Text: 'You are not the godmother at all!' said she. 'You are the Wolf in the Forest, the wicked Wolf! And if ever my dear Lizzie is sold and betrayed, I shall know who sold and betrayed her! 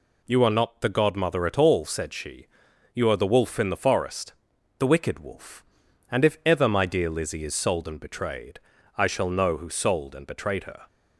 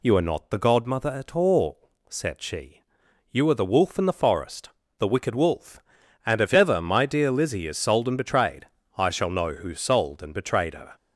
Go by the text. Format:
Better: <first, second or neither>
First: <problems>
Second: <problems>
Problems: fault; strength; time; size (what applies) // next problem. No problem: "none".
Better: neither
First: none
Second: none